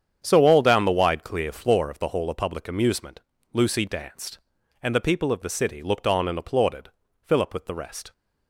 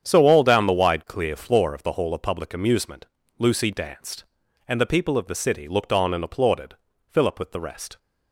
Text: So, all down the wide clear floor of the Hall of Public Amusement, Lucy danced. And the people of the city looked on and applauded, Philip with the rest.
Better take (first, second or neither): neither